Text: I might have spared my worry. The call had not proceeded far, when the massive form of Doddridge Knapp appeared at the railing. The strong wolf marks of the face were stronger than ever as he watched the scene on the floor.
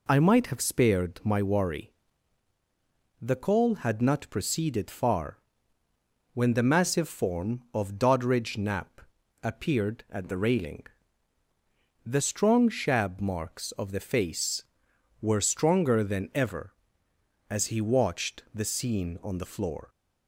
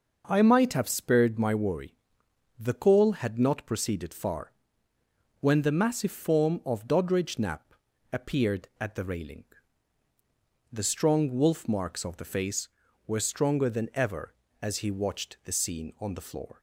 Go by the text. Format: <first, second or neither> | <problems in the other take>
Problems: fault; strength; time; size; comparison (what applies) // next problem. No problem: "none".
second | pauses between "Knapp" and "appeared"; at 9.0 s; 0.42 s long; slight in the second // says "shab" for "wolf"; at 12.6 s